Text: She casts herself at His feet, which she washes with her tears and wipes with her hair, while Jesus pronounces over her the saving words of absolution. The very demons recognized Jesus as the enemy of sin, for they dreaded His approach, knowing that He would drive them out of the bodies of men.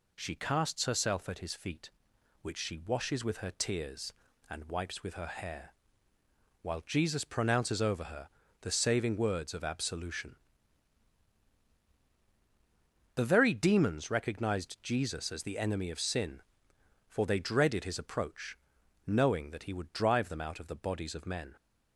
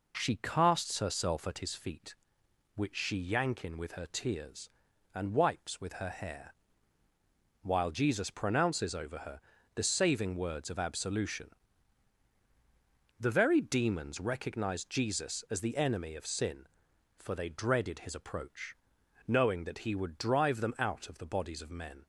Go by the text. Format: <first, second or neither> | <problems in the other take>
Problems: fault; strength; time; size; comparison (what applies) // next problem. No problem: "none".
first | says "yankin" for "washes"; at 3.1 s // pauses between "her" and "the"; slight; at 9.3 s; 0.34 s long; slight in the first